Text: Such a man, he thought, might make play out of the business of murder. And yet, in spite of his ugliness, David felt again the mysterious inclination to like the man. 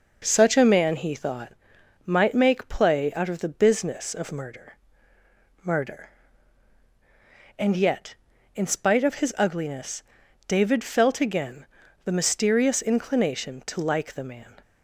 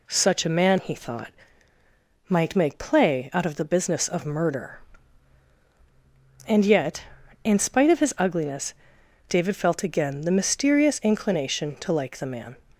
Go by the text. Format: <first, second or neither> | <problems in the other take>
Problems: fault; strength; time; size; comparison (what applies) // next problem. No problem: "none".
second | says "murder" twice; at 5.6 s // pauses between "again" and "the"; at 11.6 s; 0.40 s long